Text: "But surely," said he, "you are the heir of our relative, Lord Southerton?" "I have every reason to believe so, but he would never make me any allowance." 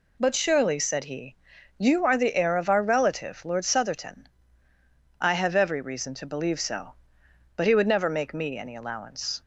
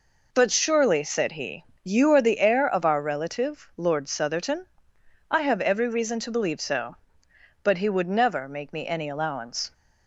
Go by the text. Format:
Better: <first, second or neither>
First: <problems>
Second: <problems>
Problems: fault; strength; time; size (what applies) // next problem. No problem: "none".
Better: neither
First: none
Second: none